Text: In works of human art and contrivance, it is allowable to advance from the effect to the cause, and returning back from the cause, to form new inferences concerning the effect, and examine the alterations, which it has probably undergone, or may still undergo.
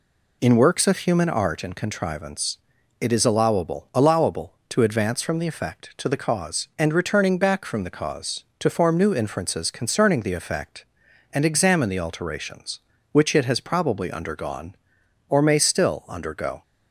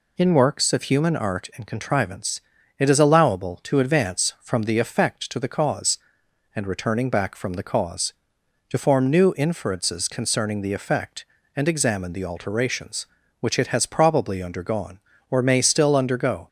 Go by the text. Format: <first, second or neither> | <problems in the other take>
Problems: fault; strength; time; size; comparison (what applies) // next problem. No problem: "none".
second | says "allowable" twice; at 3.9 s